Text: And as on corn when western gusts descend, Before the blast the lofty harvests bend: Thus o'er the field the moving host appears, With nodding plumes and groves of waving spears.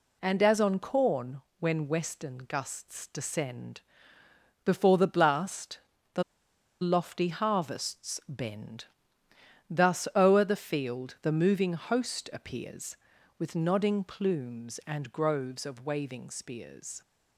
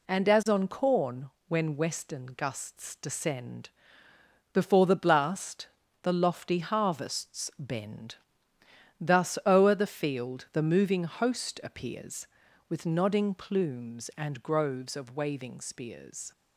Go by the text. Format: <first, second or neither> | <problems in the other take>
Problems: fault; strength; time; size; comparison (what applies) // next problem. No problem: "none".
second | pauses between "corn" and "when"; slight; at 1.4 s; 0.18 s long; slight in the second // pauses between "blast" and "the"; slight; at 5.7 s; 0.36 s long; slight in the second // pauses between "the" and "lofty"; noticeable; at 6.2 s; 0.60 s long